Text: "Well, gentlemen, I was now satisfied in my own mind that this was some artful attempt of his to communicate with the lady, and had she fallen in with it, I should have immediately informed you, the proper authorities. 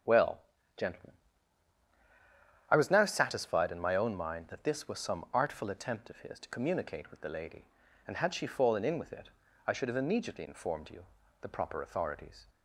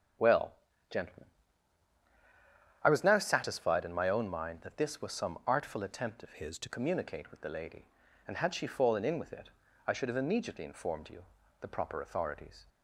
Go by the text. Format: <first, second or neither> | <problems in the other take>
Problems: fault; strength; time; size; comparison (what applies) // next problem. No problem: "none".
first | starts louder than the rest; until 3.0 s; 7 dB; also in the first // changes voice from "his" to "to"; from 6.3 to 6.6 s; 0.3 s long